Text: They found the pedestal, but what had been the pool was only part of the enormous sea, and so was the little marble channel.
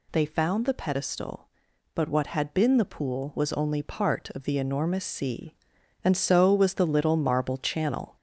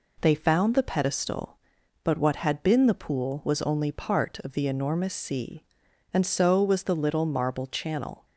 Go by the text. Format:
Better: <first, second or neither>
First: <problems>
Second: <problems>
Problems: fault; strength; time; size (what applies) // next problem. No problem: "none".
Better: second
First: gets louder; noticeable; throughout; 4 dB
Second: none